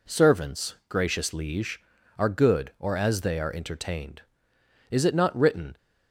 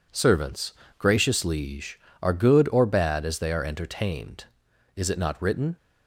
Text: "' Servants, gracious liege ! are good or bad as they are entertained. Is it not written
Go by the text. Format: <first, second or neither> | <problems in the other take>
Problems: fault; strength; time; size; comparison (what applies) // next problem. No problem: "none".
second | skips "bad"; at 2.9 s